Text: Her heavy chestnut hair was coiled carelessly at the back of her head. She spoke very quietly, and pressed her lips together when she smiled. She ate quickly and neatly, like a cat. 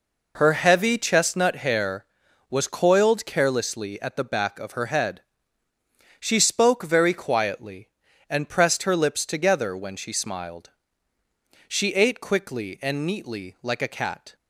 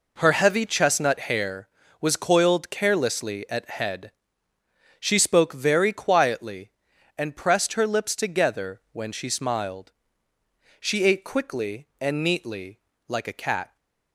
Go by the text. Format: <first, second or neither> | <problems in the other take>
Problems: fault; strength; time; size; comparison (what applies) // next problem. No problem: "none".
first | skips "the back of her"; at 3.6 s